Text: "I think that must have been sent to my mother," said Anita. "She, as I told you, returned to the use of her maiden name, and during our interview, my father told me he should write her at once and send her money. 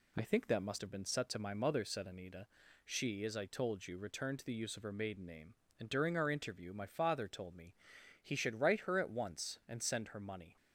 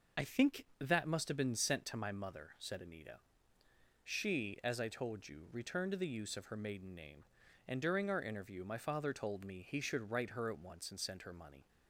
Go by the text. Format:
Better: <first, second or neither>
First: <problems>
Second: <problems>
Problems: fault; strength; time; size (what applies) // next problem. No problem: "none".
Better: second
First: says "set" for "sent"; at 1.0 s // pauses between "me" and "he"; noticeable; at 7.7 s; 0.50 s long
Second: none